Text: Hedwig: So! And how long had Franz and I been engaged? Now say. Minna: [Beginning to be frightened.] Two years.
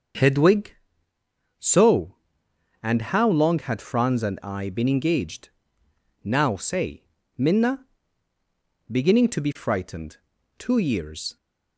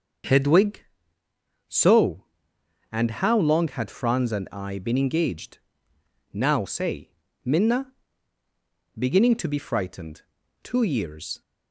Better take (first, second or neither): neither